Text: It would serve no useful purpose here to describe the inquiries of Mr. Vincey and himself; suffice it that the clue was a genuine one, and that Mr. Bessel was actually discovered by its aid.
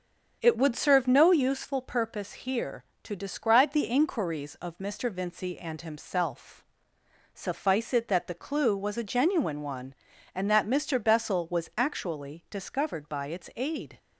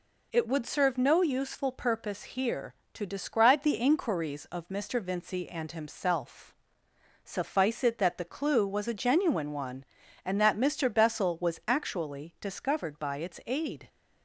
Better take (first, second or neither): second